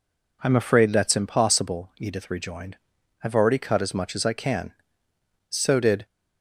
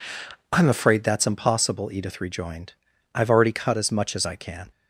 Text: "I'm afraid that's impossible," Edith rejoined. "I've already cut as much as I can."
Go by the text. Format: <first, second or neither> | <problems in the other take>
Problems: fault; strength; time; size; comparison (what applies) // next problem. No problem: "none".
second | goes on to say "So did"; from 5.4 s on; 0.56 s long